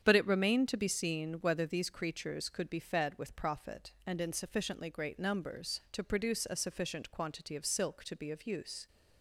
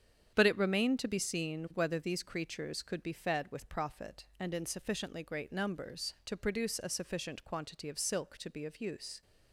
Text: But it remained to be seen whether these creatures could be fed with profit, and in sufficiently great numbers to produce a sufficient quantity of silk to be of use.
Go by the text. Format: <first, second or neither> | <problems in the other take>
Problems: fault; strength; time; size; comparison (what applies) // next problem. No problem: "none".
neither | starts louder than the rest; strong; the same in both